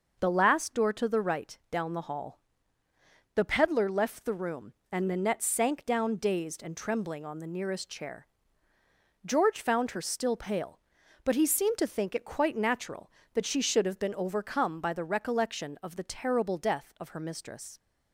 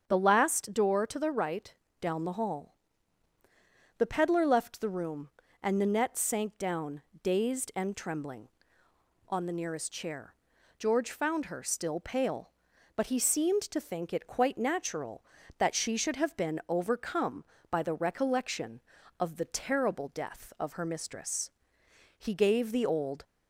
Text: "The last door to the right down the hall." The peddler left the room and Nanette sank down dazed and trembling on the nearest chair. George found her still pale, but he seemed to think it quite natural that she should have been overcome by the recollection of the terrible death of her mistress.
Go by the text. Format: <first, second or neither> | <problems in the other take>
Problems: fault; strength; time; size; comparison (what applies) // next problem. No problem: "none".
first | starts louder than the rest; strong; until 1.1 s; 8 dB // pauses between "right" and "down"; slight; at 1.7 s; 0.28 s long // pauses between "down" and "dazed"; slight; at 7.0 s; 0.22 s long // goes on to say "He gave the old"; noticeable; from 22.1 s on; 1.0 s long